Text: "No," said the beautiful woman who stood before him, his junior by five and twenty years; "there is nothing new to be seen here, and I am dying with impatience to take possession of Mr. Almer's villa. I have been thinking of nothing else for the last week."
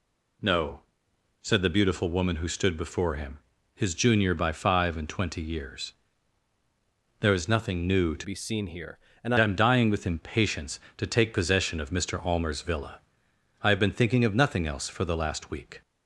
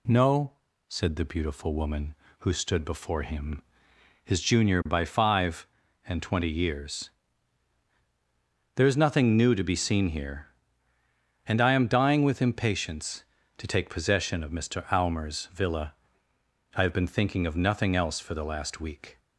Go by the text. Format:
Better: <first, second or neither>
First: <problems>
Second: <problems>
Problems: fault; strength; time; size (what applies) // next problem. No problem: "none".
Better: second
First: changes voice from "be" to "and"; from 8.2 to 9.3 s; 1.1 s long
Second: none